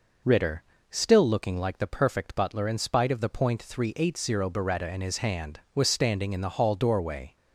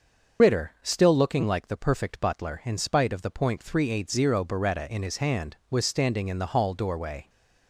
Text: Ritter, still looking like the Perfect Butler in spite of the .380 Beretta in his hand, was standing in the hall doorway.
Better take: first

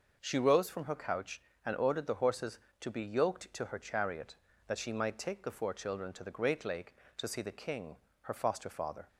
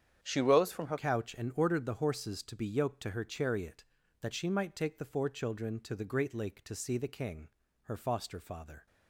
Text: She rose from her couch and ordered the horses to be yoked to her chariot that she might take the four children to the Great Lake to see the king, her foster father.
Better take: first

